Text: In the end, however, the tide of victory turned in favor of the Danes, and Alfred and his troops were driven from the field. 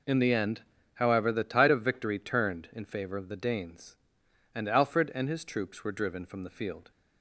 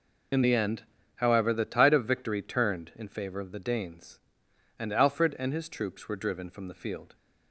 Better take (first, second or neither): first